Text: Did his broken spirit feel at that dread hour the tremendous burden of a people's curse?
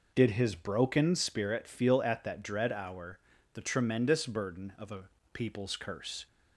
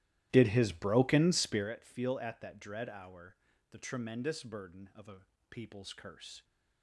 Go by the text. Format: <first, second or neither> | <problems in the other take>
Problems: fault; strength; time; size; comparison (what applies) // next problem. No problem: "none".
first | starts louder than the rest; strong; until 1.7 s; 14.5 dB // pauses between "hour" and "the"; at 3.3 s; 0.38 s long; also in the first // pauses between "a" and "people's"; slight; at 5.2 s; 0.28 s long; slight in the first